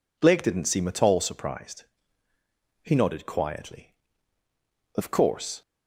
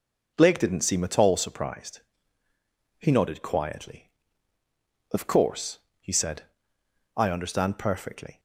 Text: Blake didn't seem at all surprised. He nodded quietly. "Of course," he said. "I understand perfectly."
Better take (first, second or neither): second